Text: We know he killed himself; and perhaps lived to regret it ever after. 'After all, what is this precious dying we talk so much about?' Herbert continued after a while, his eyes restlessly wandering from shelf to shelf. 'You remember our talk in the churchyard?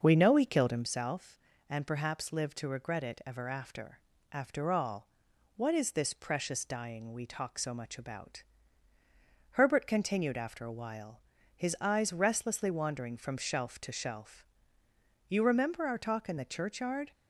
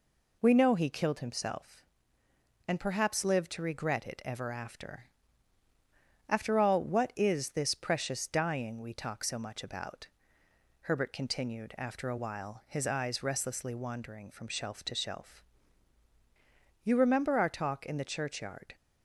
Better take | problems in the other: second | starts louder than the rest; noticeable; until 1.0 s; 6 dB

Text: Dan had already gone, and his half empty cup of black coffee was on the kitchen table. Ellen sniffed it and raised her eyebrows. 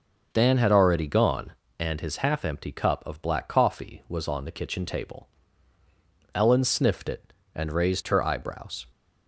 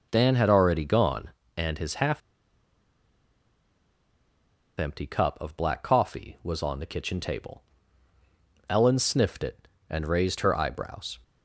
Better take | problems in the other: first | starts louder than the rest; until 1.1 s; 6 dB // pauses between "half" and "empty"; strong; at 2.2 s; 2.5 s long

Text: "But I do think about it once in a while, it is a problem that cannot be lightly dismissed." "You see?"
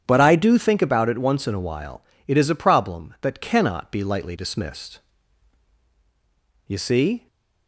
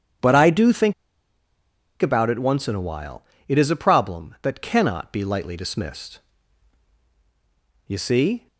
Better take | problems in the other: first | starts louder than the rest; strong; until 2.3 s; 8.5 dB; strong in the first // pauses between "think" and "about"; at 0.9 s; 1.0 s long

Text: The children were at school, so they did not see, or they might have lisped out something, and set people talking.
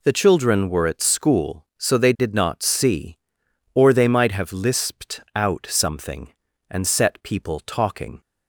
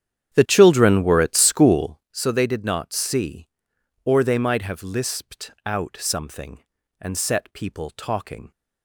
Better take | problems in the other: first | starts louder than the rest; strong; until 2.2 s; 9.5 dB

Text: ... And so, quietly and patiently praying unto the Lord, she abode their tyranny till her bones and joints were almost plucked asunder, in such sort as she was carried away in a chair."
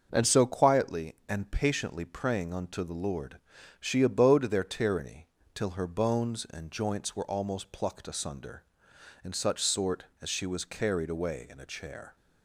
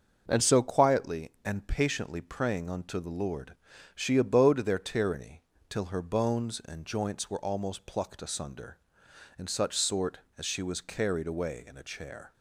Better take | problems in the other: neither | starts louder than the rest; the same in both // pauses between "tyranny" and "till"; slight; the same in both

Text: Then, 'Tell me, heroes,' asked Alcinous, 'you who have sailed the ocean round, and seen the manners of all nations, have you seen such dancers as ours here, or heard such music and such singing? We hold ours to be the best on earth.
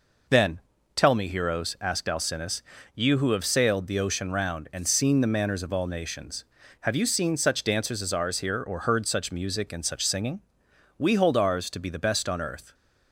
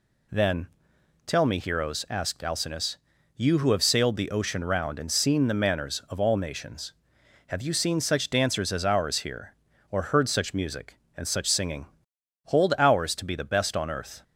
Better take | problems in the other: first | skips "We"; at 12.1 s

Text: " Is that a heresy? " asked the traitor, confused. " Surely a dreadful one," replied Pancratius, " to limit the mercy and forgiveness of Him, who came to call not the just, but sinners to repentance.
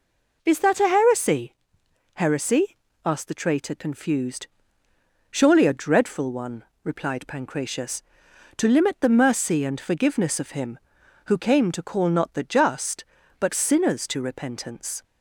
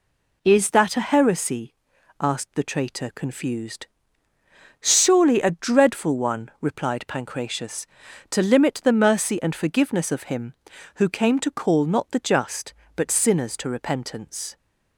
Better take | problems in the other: second | says "heresy" twice; at 2.1 s

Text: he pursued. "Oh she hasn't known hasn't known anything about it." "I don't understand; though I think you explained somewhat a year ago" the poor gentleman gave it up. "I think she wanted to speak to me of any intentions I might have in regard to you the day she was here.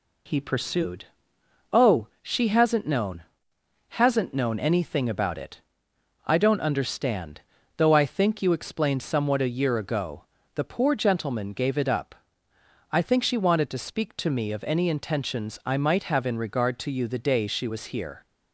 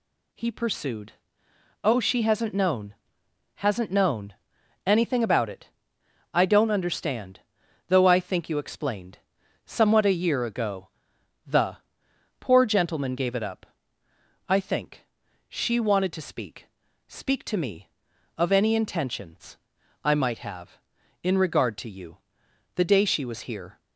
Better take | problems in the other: first | pauses between "known" and "hasn't"; noticeable; at 2.9 s; 0.62 s long; noticeable in the first // pauses between "known" and "anything"; noticeable; at 4.3 s; 0.52 s long // pauses between "explained" and "somewhat"; noticeable; at 9.1 s; 0.48 s long // pauses between "ago" and "the"; noticeable; at 10.8 s; 0.58 s long; slight in the first // pauses between "the" and "poor"; noticeable; at 11.7 s; 0.64 s long // pauses between "think" and "she"; at 15.0 s; 0.45 s long // says "speak" twice; at 17.0 s // pauses between "intentions" and "I"; noticeable; at 19.5 s; 0.48 s long // pauses between "you" and "the"; noticeable; at 22.1 s; 0.58 s long

